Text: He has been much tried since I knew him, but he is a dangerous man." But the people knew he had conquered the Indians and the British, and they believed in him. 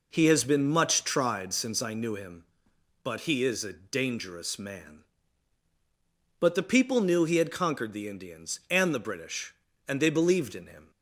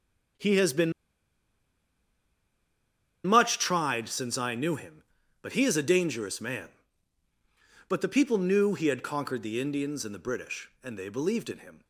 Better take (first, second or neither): first